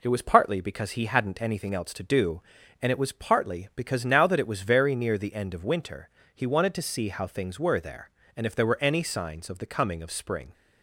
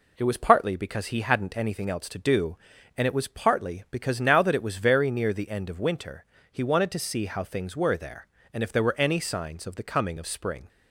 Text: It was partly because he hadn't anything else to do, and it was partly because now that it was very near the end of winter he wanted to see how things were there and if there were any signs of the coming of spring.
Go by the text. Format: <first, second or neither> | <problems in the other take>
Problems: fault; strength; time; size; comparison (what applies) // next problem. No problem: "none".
neither | pauses between "winter" and "he"; slight; the same in both